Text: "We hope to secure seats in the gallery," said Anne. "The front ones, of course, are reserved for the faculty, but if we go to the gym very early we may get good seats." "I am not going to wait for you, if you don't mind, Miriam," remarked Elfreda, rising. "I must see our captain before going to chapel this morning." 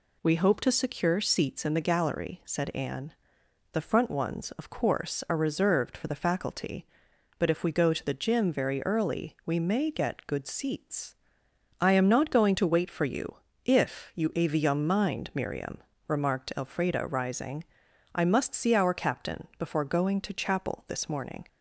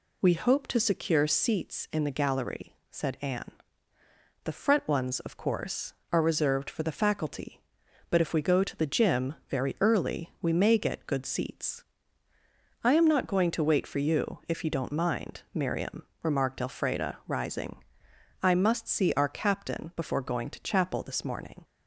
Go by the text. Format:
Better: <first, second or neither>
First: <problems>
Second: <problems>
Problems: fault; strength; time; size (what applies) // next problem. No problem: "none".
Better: second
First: says "avium" for "don't"; at 14.3 s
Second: none